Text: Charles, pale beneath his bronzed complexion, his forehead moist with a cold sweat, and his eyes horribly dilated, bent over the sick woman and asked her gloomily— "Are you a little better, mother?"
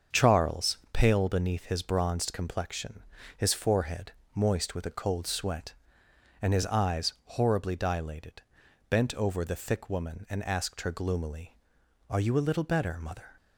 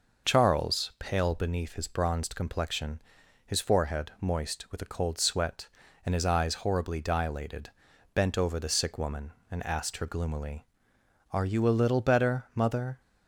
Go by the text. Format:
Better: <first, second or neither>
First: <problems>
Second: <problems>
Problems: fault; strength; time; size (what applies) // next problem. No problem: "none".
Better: second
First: starts louder than the rest; until 1.2 s; 7 dB // pauses between "forehead" and "moist"; slight; at 4.1 s; 0.24 s long // says "thick" for "sick"; at 9.5 s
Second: none